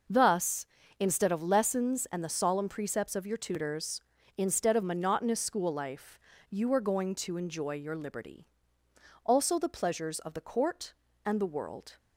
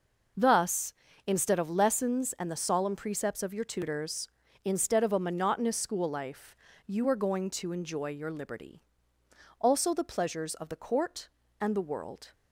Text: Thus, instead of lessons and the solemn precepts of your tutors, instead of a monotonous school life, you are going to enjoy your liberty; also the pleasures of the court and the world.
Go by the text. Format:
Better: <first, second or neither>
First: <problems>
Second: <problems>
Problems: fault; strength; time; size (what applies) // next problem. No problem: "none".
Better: second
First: skips "a"; at 4.8 s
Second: none